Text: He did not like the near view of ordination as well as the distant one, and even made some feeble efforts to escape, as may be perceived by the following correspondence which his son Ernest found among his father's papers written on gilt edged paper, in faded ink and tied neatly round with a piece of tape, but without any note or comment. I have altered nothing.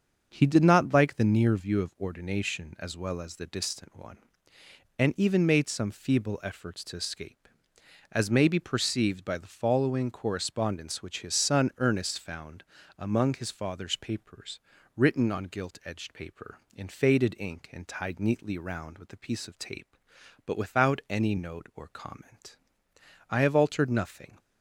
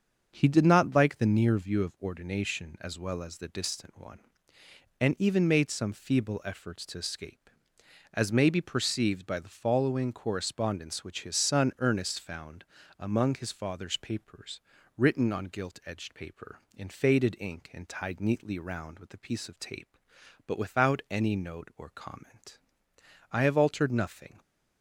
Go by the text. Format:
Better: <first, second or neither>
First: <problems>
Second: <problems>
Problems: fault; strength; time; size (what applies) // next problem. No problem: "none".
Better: neither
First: starts louder than the rest; until 1.3 s; 6.5 dB // pauses between "found" and "among"; slight; at 12.6 s; 0.34 s long // pauses between "papers" and "written"; slight; at 14.6 s; 0.34 s long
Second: starts louder than the rest; until 1.3 s; 6.5 dB // pauses between "found" and "among"; slight; at 12.6 s; 0.34 s long // pauses between "papers" and "written"; slight; at 14.6 s; 0.34 s long